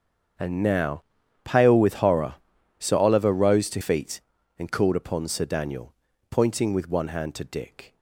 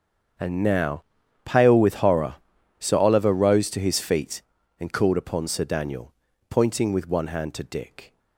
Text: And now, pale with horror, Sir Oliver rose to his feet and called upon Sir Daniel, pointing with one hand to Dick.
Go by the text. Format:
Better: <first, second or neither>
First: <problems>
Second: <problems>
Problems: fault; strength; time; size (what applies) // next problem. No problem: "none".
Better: second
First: starts louder than the rest; strong; until 1.8 s; 7 dB // skips "his"; at 3.7 s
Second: starts louder than the rest; strong; until 1.8 s; 7.5 dB